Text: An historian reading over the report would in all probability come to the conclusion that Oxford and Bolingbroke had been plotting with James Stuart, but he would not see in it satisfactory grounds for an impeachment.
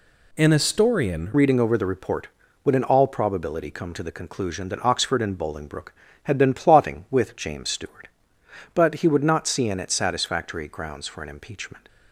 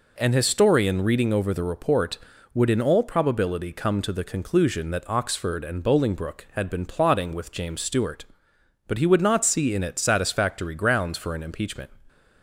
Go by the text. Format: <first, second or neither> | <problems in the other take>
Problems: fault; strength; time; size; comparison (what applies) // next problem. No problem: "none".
second | changes voice at "reading"; from 1.3 s on; 10.5 s long